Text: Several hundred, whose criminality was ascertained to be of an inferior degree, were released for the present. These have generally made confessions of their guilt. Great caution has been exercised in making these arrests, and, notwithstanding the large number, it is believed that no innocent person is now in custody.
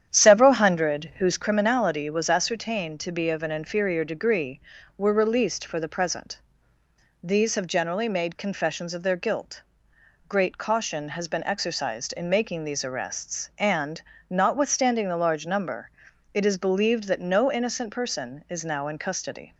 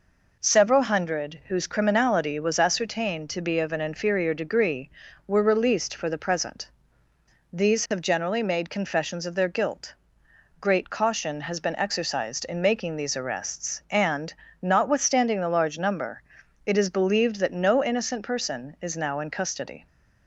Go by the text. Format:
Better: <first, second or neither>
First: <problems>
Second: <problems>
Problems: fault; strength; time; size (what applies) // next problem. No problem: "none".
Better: second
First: starts louder than the rest; strong; until 1.6 s; 9.5 dB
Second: none